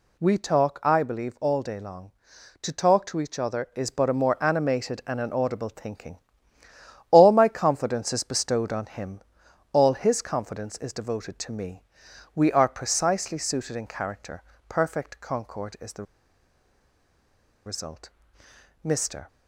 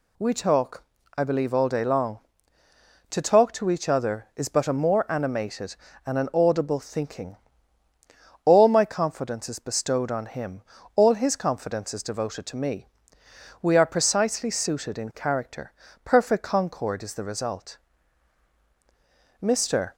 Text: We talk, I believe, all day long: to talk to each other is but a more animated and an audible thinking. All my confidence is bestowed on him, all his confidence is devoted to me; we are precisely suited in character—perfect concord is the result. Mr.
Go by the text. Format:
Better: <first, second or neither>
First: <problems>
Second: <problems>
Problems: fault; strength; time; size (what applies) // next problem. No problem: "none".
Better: second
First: pauses between "the" and "result"; strong; at 16.0 s; 1.6 s long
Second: none